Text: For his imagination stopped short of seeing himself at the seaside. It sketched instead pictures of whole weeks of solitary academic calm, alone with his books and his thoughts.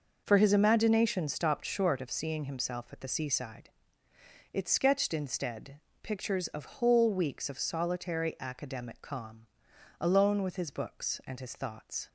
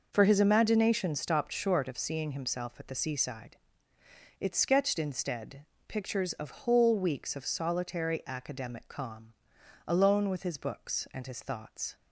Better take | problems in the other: neither | pauses between "instead" and "pictures"; slight; the same in both

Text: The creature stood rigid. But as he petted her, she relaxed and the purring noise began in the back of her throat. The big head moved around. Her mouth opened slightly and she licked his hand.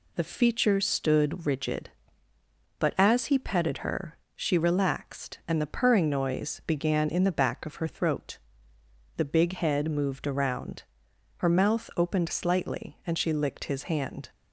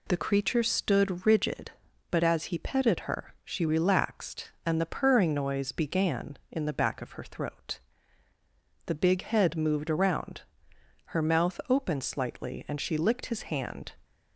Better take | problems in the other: second | says "feature" for "creature"; at 0.2 s

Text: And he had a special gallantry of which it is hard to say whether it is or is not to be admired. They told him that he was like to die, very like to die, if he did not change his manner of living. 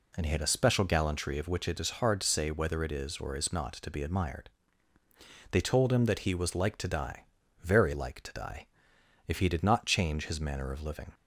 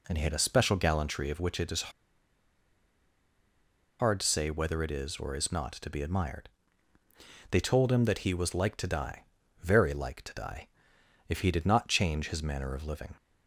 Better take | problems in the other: first | pauses between "is" and "hard"; strong; at 1.8 s; 2.0 s long

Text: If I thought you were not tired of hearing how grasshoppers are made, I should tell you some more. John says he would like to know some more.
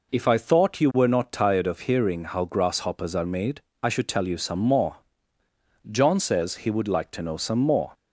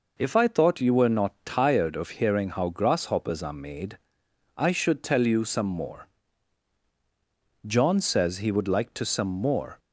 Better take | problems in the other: first | skips "know"; at 9.0 s

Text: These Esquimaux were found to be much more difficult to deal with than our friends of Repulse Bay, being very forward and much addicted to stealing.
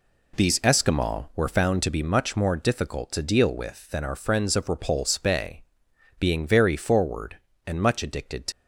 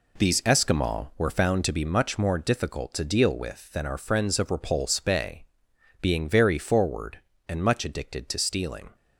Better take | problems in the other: second | stops before "stealing"; at 8.5 s

